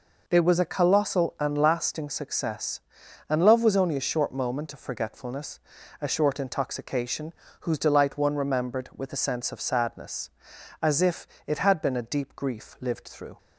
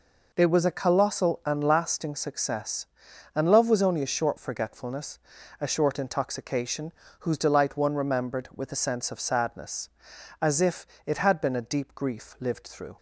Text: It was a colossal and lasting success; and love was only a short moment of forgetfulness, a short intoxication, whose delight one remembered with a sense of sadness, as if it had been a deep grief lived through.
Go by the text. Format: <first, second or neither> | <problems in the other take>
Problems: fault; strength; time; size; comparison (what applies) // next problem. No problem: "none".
first | skips "moment of"; at 4.3 s // pauses between "if" and "it"; slight; at 10.8 s; 0.18 s long; slight in the first